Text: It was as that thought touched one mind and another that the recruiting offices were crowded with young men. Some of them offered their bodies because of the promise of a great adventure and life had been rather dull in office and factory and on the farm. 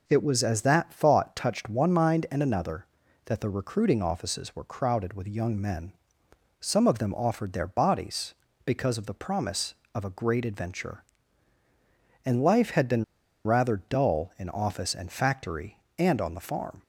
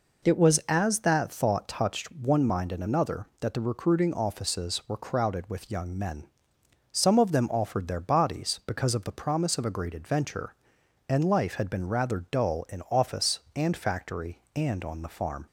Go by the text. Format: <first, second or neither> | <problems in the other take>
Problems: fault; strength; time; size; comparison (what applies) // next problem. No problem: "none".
second | pauses between "been" and "rather"; at 13.0 s; 0.41 s long